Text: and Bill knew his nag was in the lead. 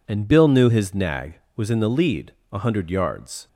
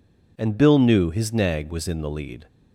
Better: second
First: goes on to say "A hundred yards"; noticeable; from 2.5 s on; 0.96 s long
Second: none

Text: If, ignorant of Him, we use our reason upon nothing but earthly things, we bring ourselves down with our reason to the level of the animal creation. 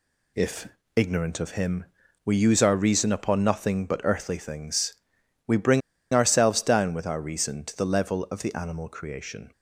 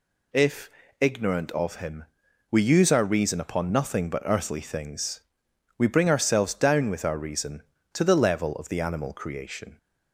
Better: second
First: pauses between "bring" and "ourselves"; slight; at 5.8 s; 0.33 s long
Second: none

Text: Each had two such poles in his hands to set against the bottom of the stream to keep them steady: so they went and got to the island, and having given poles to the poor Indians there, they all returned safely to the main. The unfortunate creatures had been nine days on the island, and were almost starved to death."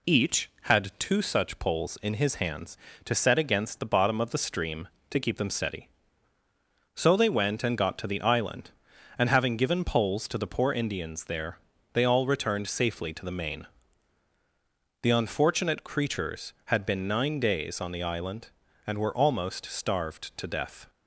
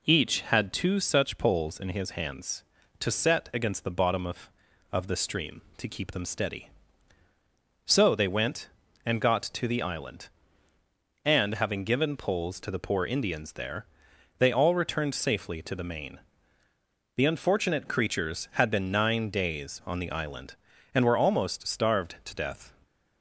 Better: first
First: none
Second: says "of" twice; at 4.9 s

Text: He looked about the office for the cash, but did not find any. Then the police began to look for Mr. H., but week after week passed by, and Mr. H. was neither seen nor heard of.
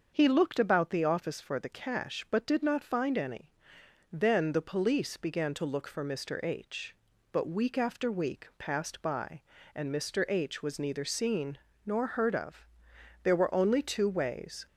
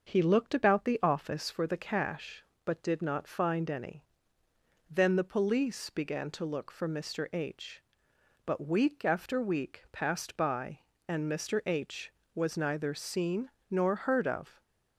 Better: second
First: starts louder than the rest; until 1.1 s; 6.5 dB // pauses between "seen" and "nor"; slight; at 11.5 s; 0.30 s long // goes on to say "There were only two ways"; from 13.2 s on; 1.4 s long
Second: starts louder than the rest; until 1.1 s; 6.5 dB // pauses between "seen" and "nor"; slight; at 13.4 s; 0.20 s long

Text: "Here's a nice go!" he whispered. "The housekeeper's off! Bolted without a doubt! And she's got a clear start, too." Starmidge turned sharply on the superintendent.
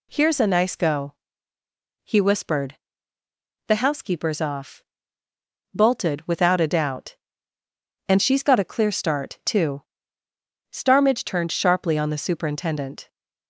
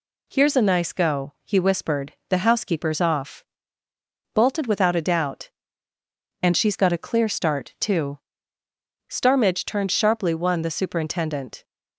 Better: first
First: none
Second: says "one" for "on"; at 10.3 s

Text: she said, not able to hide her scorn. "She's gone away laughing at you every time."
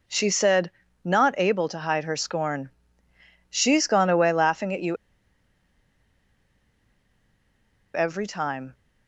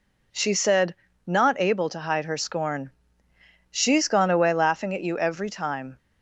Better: second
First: pauses between "you" and "every"; strong; at 4.9 s; 2.9 s long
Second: none

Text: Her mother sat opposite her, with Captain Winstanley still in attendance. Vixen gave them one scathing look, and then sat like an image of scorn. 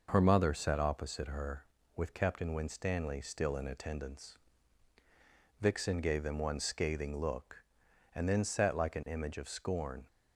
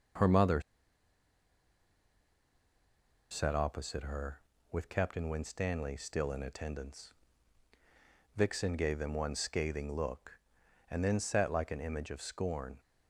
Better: first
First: none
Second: pauses between "mother" and "sat"; strong; at 0.6 s; 2.6 s long

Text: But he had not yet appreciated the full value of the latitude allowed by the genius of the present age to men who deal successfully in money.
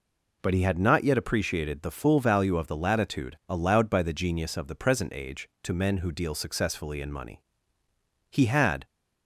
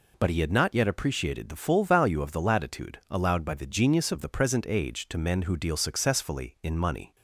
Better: second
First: goes on to say "He had"; from 8.2 s on; 0.56 s long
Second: none

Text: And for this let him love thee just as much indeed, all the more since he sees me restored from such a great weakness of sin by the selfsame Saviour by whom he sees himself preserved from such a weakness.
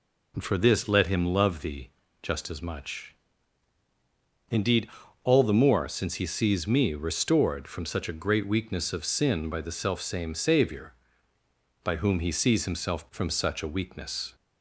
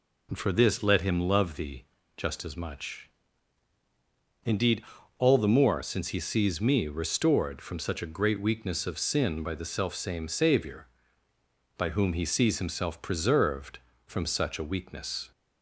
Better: second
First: pauses between "thee" and "just"; slight; at 1.8 s; 0.32 s long // pauses between "much" and "indeed"; strong; at 3.1 s; 1.3 s long // skips "preserved"; at 13.0 s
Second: pauses between "thee" and "just"; slight; at 1.8 s; 0.32 s long // pauses between "much" and "indeed"; strong; at 3.0 s; 1.3 s long

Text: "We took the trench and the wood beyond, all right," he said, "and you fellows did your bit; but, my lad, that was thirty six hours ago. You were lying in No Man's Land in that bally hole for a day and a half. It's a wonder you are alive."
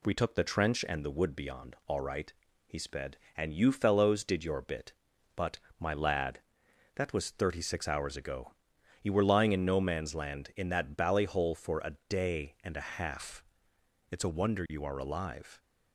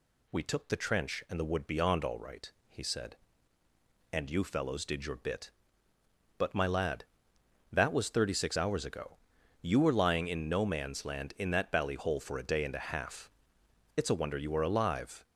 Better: second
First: says "sped" for "said"; at 2.7 s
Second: none

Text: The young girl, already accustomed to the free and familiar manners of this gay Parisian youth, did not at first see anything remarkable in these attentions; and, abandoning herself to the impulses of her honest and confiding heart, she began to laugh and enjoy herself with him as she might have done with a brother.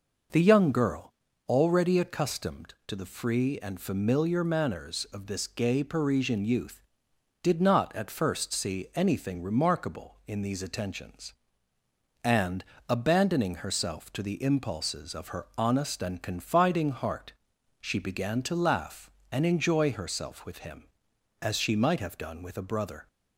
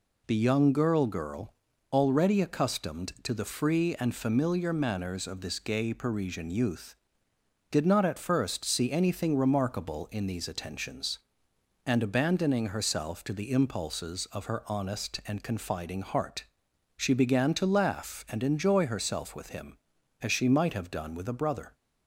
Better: first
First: none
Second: says "girl" twice; at 1.0 s

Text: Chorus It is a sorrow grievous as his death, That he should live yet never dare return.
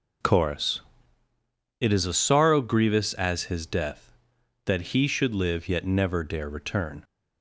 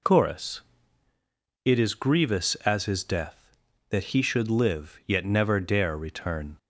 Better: first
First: pauses between "Chorus" and "It"; noticeable; at 0.8 s; 0.98 s long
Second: pauses between "Chorus" and "It"; at 0.5 s; 1.0 s long // skips "a sorrow"; at 1.9 s

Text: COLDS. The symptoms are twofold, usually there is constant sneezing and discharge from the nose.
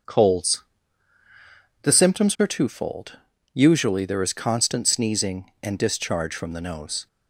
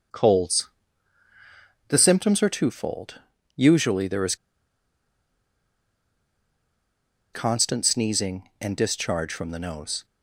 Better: first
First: none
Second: starts louder than the rest; until 2.2 s; 6.5 dB // pauses between "is" and "constant"; strong; at 4.3 s; 2.9 s long

